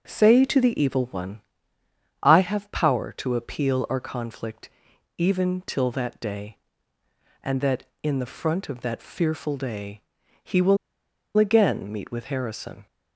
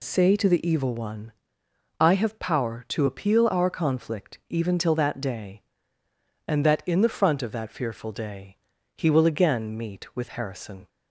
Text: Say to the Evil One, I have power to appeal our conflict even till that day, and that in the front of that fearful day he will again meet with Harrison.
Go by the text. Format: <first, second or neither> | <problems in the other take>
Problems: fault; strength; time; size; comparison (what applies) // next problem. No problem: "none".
second | starts louder than the rest; noticeable; until 1.0 s; 6 dB // pauses between "conflict" and "even"; noticeable; at 4.7 s; 0.48 s long // pauses between "day" and "he"; at 10.0 s; 0.42 s long; also in the second // pauses between "will" and "again"; noticeable; at 10.7 s; 0.61 s long